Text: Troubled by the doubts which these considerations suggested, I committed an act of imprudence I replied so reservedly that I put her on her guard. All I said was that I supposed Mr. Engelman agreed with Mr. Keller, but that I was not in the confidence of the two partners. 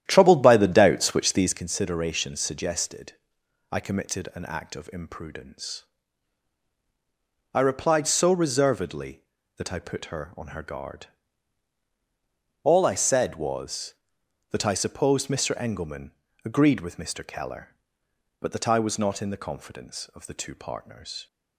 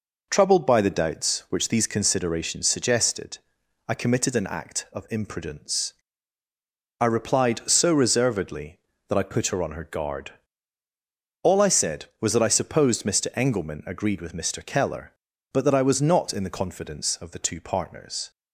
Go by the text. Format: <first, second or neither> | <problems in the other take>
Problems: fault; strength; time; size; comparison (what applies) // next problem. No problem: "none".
second | starts louder than the rest; strong; until 1.7 s; 11 dB // pauses between "imprudence" and "I"; strong; at 5.8 s; 1.6 s long; also in the second // pauses between "Engelman" and "agreed"; slight; at 16.1 s; 0.32 s long